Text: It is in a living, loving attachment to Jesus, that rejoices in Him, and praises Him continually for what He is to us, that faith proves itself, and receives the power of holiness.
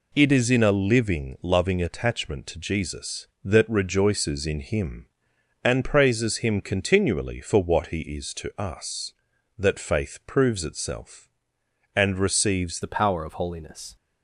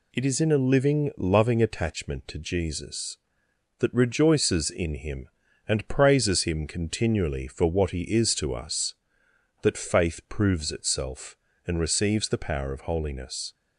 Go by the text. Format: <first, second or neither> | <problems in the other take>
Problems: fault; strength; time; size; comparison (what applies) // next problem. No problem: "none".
second | changes voice at "the"; from 12.8 s on; 1.1 s long